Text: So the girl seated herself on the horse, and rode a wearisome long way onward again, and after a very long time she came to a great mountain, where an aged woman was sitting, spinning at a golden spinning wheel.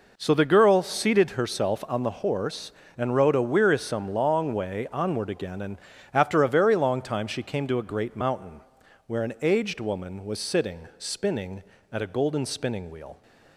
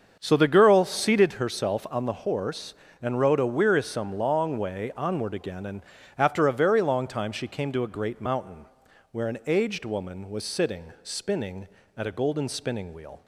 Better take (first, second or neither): first